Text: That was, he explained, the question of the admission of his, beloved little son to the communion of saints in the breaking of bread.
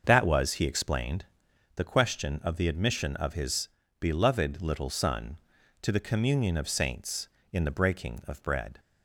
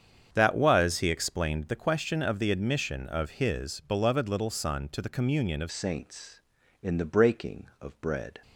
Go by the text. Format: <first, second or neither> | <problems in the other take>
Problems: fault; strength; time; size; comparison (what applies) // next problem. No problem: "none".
first | starts louder than the rest; strong; until 1.3 s; 8 dB; also in the first // changes voice at "saints"; from 5.7 s on; 2.7 s long